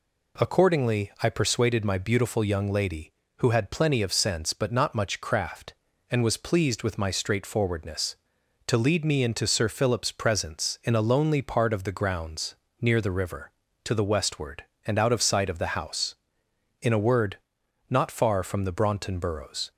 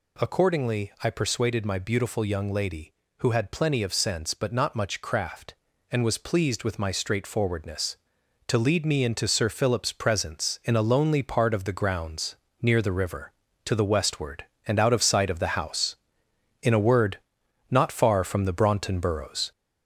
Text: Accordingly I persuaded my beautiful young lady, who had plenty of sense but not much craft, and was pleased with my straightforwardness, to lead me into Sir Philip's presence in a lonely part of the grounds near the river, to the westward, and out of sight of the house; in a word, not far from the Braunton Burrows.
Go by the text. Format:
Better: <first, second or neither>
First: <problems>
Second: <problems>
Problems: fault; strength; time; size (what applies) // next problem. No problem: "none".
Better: first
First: pauses between "grounds" and "near"; slight; at 12.5 s; 0.28 s long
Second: gets louder; noticeable; throughout; 4 dB // pauses between "grounds" and "near"; slight; at 12.3 s; 0.28 s long